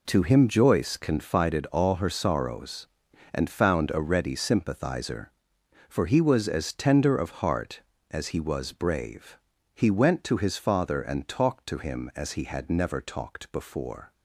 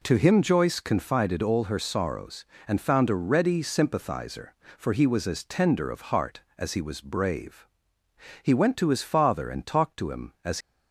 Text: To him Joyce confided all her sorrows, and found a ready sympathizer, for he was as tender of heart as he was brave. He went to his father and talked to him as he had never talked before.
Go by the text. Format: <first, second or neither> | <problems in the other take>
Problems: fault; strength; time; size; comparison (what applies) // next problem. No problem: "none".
first | stops before "he had never talked before"; at 10.6 s